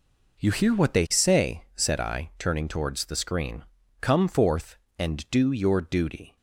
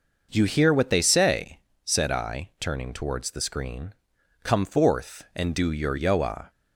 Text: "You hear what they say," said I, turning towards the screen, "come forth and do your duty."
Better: first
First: none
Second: says "yoa" for "duty"; at 5.9 s

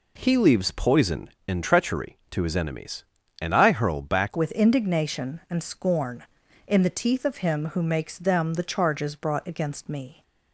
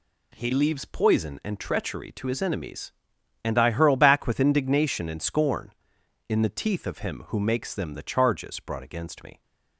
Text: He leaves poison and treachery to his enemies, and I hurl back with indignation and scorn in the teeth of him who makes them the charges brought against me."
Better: second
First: changes voice at "with"; from 4.3 s on; 5.9 s long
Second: none

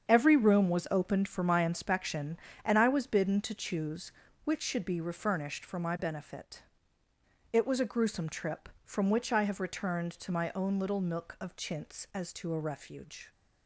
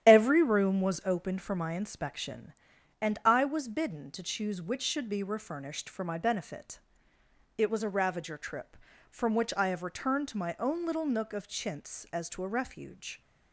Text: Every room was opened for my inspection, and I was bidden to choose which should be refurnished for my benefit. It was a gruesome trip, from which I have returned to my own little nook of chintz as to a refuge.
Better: first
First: starts louder than the rest; strong; until 1.1 s; 7.5 dB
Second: starts louder than the rest; strong; until 1.1 s; 10.5 dB // says "ravager" for "gruesome"; at 7.8 s

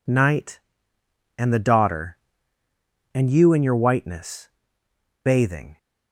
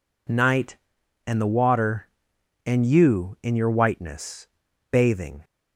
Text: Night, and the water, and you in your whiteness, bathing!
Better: second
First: says "daughter" for "water"; at 1.5 s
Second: none

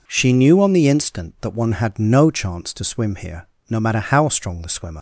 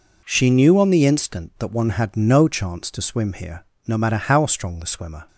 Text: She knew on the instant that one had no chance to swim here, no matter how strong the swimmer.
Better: second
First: leaves "swimmer" unfinished; at 4.9 s; 90 ms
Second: none

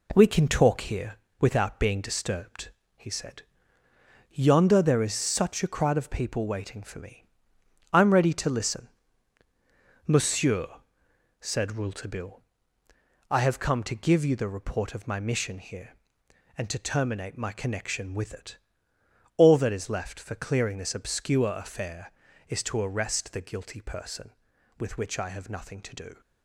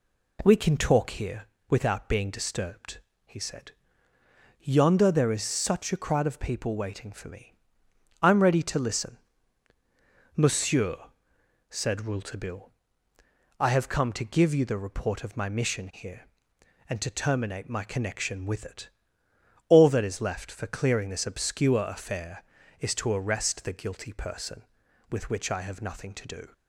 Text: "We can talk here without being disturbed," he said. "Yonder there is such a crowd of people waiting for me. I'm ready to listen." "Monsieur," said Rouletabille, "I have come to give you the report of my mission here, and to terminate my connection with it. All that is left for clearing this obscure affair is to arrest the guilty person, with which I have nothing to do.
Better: second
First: gets quieter; noticeable; throughout; 5.5 dB // pauses between "here" and "without"; slight; at 1.1 s; 0.24 s long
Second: pauses between "here" and "without"; slight; at 1.4 s; 0.24 s long

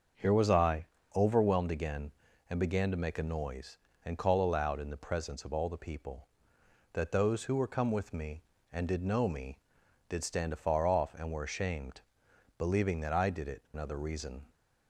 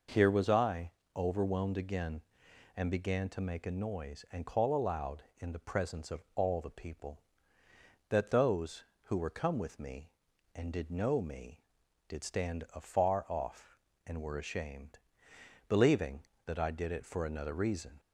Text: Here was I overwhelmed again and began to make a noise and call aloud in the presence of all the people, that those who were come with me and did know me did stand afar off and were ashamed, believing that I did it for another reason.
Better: second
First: starts louder than the rest; until 1.4 s; 6.5 dB // pauses between "I" and "overwhelmed"; slight; at 0.8 s; 0.28 s long // skips "for"; at 13.6 s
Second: pauses between "I" and "overwhelmed"; slight; at 0.8 s; 0.26 s long

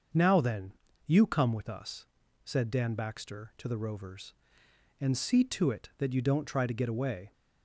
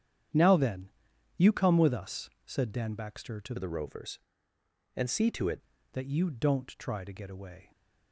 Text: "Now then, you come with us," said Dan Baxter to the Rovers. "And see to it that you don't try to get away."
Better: first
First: starts louder than the rest; until 1.4 s; 6.5 dB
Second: starts louder than the rest; strong; until 1.8 s; 9 dB // changes voice from "the" to "it"; from 3.5 to 5.5 s; 2.0 s long

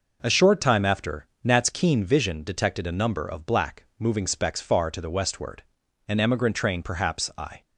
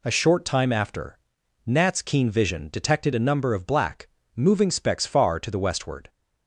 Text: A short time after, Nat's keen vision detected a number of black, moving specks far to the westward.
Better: second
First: goes on to say "An emigrant train perhaps I"; from 6.0 s on; 1.5 s long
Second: none

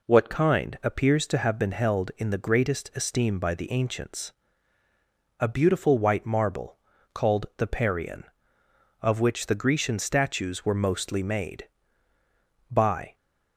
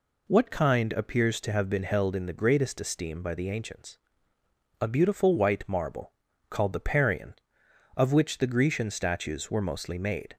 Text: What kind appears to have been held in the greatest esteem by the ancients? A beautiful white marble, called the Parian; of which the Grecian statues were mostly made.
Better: second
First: goes on to say "By"; slight; from 12.6 s on; 0.46 s long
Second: none

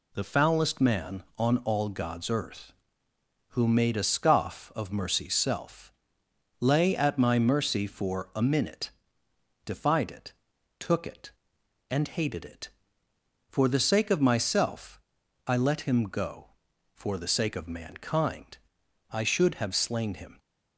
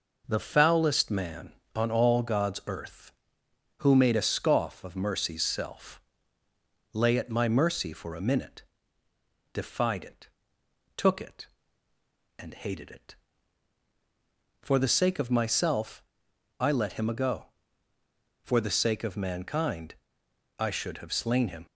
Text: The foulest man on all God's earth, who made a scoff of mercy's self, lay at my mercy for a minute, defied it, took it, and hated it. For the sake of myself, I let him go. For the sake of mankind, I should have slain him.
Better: first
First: none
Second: says "ago" for "go"; at 17.0 s

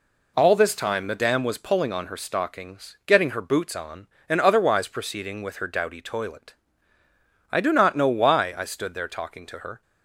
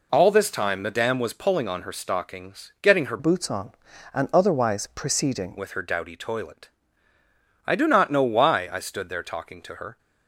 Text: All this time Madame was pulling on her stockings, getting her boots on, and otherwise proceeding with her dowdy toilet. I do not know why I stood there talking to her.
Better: first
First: none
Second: changes voice from "boots" to "proceeding"; from 3.1 to 5.5 s; 2.4 s long

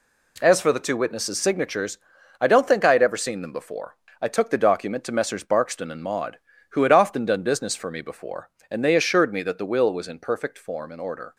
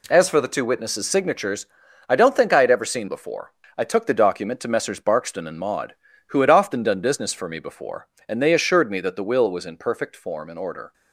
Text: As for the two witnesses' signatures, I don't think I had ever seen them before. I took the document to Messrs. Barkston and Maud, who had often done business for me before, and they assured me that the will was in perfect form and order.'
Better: first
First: none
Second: skips "them"; at 3.0 s

